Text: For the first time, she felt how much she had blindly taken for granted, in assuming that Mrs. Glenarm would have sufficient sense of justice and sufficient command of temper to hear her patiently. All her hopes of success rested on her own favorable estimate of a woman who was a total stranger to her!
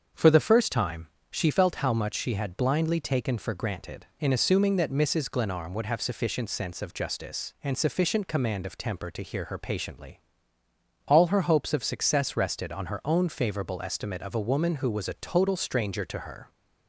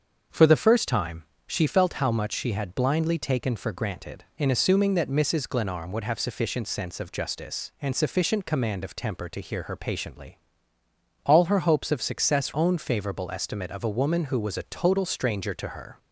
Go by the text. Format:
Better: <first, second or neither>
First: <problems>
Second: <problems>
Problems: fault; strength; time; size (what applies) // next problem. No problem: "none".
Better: first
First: starts louder than the rest; until 1.3 s; 7 dB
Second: starts louder than the rest; until 1.5 s; 7 dB // skips "rested on her"; at 12.5 s